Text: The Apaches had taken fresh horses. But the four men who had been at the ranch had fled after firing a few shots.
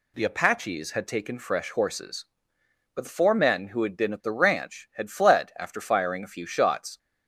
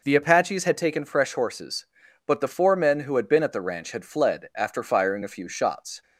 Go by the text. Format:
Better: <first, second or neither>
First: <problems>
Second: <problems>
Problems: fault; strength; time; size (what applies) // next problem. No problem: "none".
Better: neither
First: none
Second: none